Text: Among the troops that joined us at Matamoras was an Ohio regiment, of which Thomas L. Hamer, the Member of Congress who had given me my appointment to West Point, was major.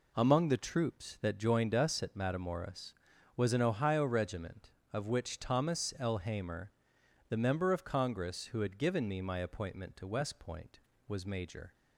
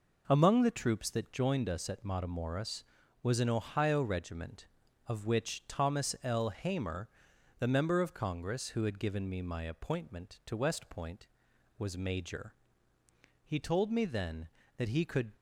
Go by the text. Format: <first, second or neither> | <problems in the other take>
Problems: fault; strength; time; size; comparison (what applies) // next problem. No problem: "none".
first | goes on to say "He told me then that he could"; strong; from 13.4 s on; 1.8 s long